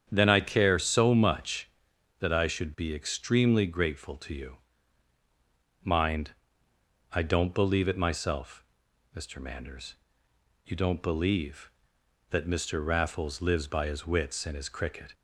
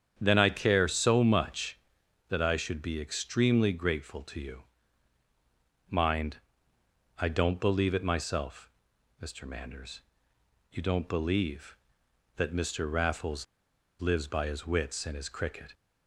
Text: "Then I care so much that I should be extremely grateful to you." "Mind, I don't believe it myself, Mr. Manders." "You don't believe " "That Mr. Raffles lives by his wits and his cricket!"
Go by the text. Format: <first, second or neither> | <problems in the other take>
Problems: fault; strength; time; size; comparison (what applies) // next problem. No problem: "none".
first | starts louder than the rest; strong; until 1.2 s; 8.5 dB; strong in the first // pauses between "Raffles" and "lives"; noticeable; at 13.4 s; 0.54 s long